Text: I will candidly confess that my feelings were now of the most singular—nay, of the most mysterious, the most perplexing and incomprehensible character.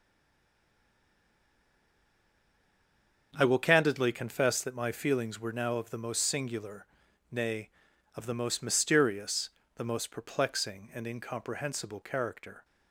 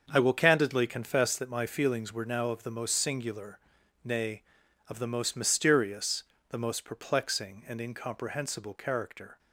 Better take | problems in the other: second | stays silent before the first word; strong; until 3.3 s; 3.3 s long // starts louder than the rest; until 4.3 s; 6.5 dB; also in the second

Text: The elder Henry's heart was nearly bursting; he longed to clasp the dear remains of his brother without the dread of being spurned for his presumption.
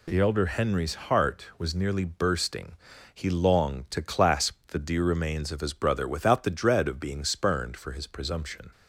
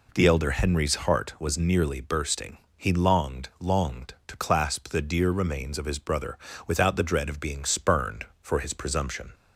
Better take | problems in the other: first | says "longed" twice; at 3.5 s // pauses between "brother" and "without"; slight; at 6.3 s; 0.30 s long

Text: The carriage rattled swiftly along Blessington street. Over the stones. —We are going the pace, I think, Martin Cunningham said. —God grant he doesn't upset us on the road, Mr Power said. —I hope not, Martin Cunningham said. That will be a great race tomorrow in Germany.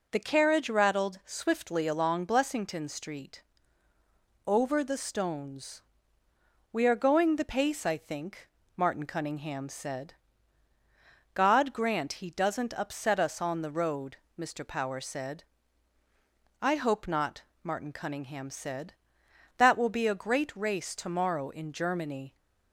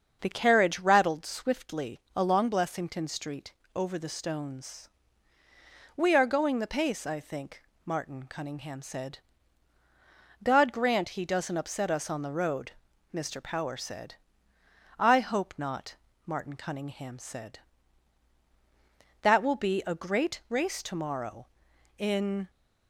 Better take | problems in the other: first | starts louder than the rest; until 1.2 s; 7 dB // pauses between "swiftly" and "along"; slight; at 1.9 s; 0.16 s long // stops before "Germany"; at 22.5 s

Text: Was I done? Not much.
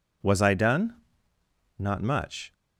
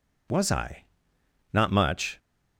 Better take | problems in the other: first | skips "done"; at 1.1 s

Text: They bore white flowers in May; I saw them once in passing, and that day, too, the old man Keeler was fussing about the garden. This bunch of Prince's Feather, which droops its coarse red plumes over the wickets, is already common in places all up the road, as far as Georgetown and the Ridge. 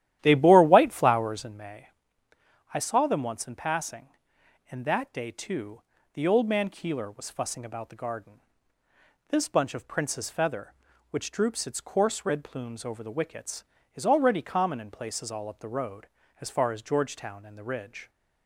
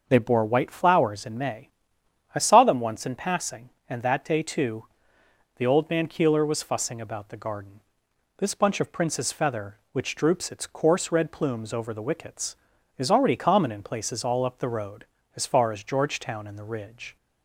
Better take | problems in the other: second | starts louder than the rest; strong; until 1.6 s; 12.5 dB

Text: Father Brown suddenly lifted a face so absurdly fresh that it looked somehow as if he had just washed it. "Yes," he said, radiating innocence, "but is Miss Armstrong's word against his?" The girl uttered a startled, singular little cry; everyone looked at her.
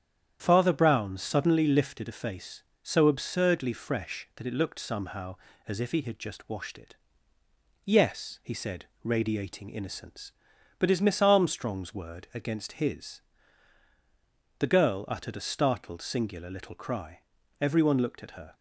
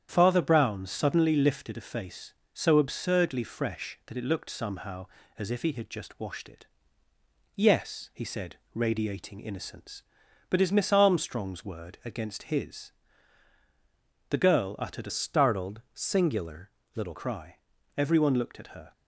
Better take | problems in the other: first | starts louder than the rest; strong; until 1.1 s; 9 dB; strong in the first // changes voice from "startled" to "little"; from 15.0 to 17.1 s; 2.1 s long // pauses between "singular" and "little"; slight; at 16.7 s; 0.22 s long

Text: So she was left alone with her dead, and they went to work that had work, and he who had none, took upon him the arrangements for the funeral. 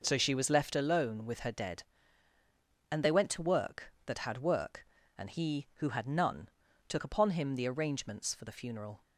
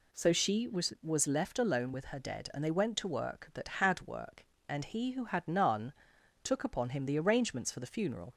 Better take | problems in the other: first | says "was" twice; at 1.0 s

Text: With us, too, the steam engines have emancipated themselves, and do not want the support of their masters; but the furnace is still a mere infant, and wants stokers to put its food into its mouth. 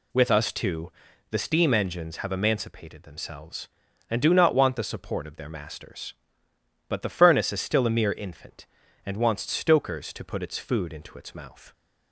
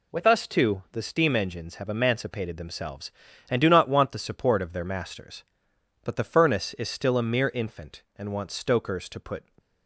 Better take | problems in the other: first | stops before "its food into its mouth"; at 9.5 s

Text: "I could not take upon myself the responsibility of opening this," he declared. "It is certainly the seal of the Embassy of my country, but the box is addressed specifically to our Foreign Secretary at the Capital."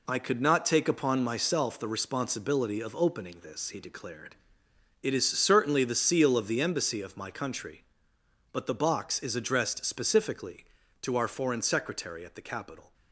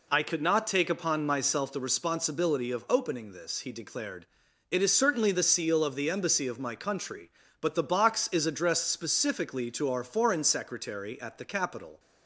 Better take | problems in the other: second | gets quieter; throughout; 7 dB

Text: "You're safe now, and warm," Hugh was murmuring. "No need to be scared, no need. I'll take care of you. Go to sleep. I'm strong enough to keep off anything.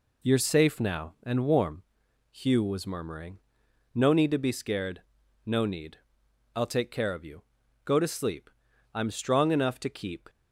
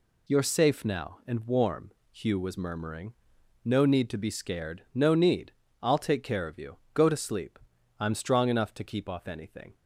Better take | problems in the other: second | stops before "off anything"; at 10.2 s

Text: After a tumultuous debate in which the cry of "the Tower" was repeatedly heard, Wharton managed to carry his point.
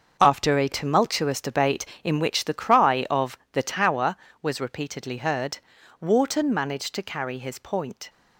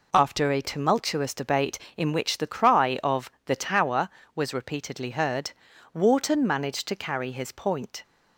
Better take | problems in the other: second | gets quieter; strong; throughout; 10.5 dB

